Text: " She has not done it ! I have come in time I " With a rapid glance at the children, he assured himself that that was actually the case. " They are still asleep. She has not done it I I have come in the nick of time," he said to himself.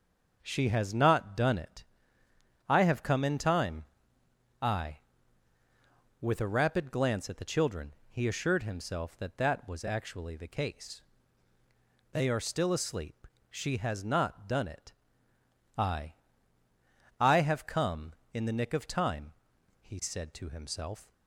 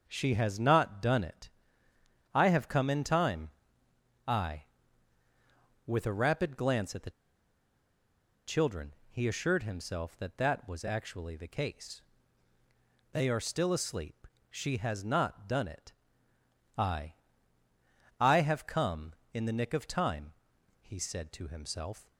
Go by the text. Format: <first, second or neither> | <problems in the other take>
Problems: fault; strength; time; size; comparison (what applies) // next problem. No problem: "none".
first | starts louder than the rest; until 1.0 s; 6.5 dB; also in the first // pauses between "time" and "I"; noticeable; at 3.5 s; 0.74 s long; noticeable in the first // pauses between "the" and "children"; strong; at 7.1 s; 1.3 s long // pauses between "it" and "I"; noticeable; at 15.9 s; 0.84 s long; noticeable in the first // pauses between "I" and "I"; at 17.1 s; 1.0 s long; also in the first